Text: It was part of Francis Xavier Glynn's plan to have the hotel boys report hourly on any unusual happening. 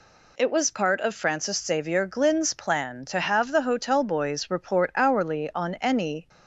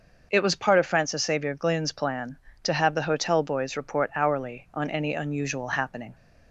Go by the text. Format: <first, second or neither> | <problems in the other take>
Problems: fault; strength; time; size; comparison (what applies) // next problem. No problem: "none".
second | stops before "unusual happening"; at 6.2 s